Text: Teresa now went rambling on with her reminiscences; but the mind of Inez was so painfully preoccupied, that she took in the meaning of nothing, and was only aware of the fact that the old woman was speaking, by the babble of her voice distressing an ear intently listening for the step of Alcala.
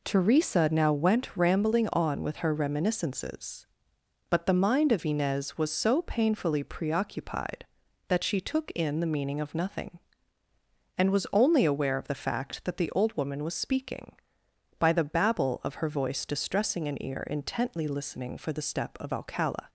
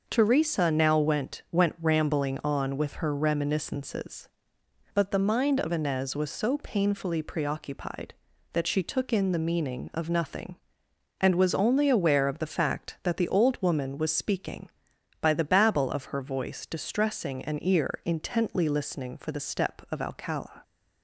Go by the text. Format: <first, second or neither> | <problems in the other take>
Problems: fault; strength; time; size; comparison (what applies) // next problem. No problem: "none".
first | says "went" twice; at 1.5 s